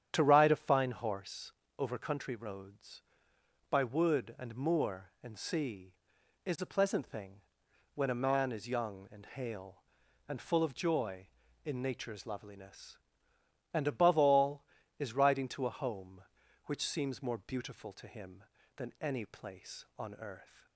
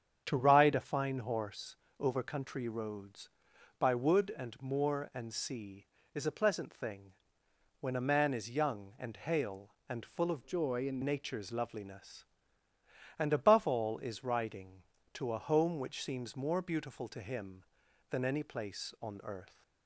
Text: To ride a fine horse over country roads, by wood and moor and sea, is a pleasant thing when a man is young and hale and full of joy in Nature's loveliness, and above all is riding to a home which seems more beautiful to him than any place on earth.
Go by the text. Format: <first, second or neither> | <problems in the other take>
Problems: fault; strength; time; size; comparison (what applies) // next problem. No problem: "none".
first | starts louder than the rest; strong; until 1.2 s; 8 dB; strong in the first // pauses between "horse" and "over"; slight; at 1.7 s; 0.24 s long; slight in the first // pauses between "thing" and "when"; noticeable; at 7.1 s; 0.68 s long; noticeable in the first // changes voice from "joy" to "in"; from 10.4 to 11.0 s; 0.6 s long